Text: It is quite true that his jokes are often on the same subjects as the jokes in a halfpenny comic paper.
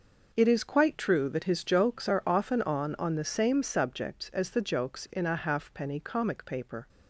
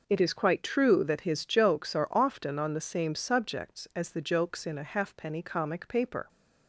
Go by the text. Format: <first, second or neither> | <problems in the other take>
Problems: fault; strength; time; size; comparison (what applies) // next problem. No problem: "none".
second | says "on" twice; at 2.9 s